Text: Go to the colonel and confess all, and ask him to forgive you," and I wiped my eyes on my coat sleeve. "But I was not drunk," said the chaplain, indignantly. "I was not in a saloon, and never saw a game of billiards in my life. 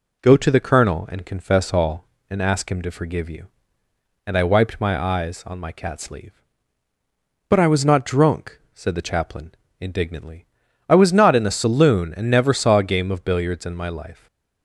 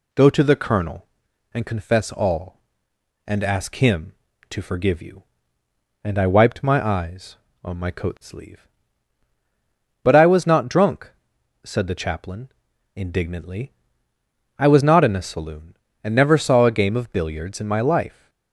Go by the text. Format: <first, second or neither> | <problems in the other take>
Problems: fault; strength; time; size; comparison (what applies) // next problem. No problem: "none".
second | says "cat" for "coat"; at 5.7 s // stays silent after the last word; slight; from 14.1 s on; 0.5 s long